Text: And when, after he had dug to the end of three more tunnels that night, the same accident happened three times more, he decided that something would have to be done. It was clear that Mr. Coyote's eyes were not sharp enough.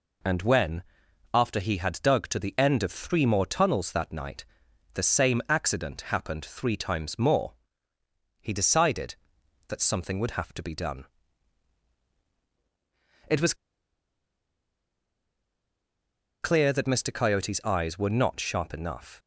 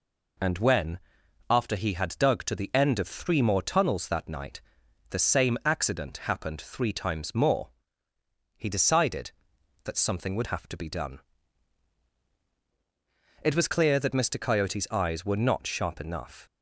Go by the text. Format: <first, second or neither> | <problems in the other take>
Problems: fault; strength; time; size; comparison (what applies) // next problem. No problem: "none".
second | pauses between "was" and "clear"; strong; at 13.5 s; 2.8 s long